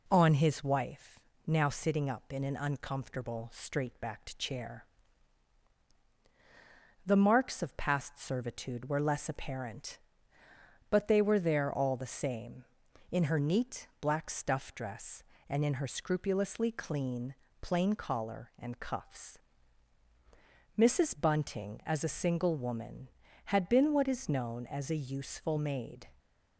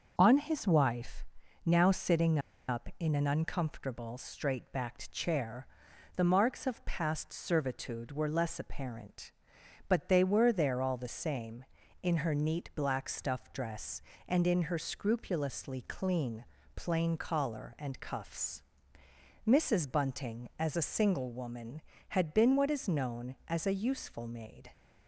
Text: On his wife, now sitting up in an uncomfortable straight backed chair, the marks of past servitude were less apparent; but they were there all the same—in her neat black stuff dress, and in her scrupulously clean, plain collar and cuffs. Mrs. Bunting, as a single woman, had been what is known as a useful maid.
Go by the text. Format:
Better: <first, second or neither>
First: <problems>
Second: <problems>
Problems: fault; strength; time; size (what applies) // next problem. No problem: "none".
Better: first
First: none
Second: starts louder than the rest; noticeable; until 1.1 s; 6 dB // pauses between "sitting" and "up"; slight; at 2.3 s; 0.30 s long